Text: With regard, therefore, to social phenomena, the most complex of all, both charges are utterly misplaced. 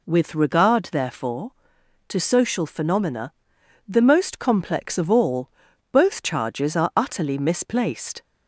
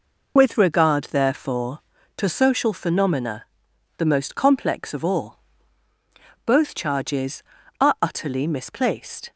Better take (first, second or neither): first